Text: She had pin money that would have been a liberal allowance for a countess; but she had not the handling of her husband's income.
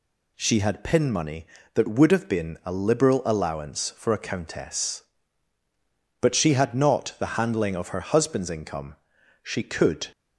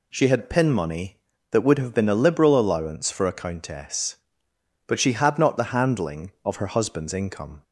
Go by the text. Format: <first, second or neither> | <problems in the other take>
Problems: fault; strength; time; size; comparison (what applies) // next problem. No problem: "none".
second | goes on to say "She could"; noticeable; from 9.4 s on; 0.64 s long